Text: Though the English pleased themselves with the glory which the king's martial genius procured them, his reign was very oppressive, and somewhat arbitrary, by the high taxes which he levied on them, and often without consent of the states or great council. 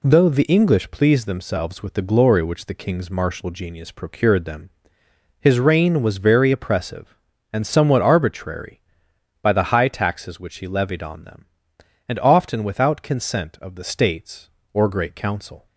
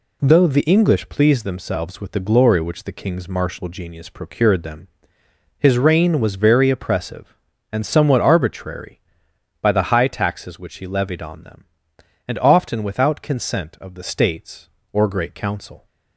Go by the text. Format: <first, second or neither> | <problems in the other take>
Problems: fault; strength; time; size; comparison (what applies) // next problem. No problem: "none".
neither | none